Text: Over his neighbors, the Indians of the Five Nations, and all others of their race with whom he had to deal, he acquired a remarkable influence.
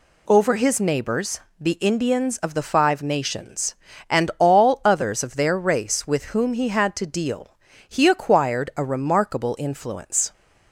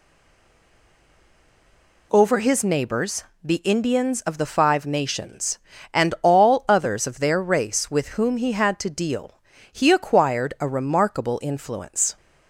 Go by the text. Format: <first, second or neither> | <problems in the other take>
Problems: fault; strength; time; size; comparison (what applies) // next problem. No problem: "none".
first | stays silent before the first word; noticeable; until 2.1 s; 2.1 s long